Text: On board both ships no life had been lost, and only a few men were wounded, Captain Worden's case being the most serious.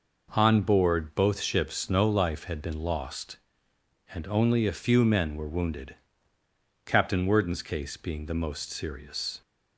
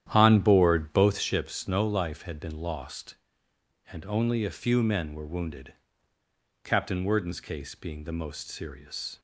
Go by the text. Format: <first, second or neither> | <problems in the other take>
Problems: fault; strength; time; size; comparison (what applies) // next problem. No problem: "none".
first | starts louder than the rest; strong; until 1.4 s; 10.5 dB